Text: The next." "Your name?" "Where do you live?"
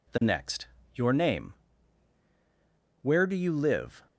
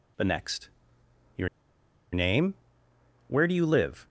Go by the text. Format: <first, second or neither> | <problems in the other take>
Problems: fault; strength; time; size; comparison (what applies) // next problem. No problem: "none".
first | pauses between "Your" and "name"; noticeable; at 1.4 s; 0.64 s long